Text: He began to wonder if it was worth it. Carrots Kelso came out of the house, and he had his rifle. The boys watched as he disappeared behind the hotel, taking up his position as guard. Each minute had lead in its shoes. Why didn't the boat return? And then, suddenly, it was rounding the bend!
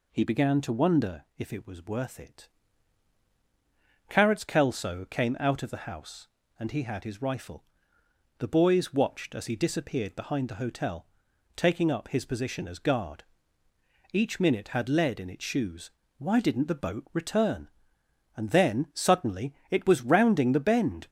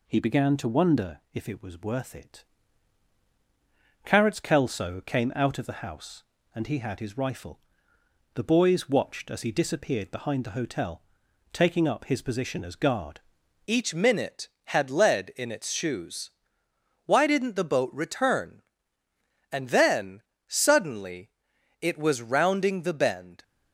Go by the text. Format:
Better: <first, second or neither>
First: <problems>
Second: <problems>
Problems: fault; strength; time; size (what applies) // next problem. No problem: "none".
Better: first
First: none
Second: changes voice at "Each"; from 13.6 s on; 9.8 s long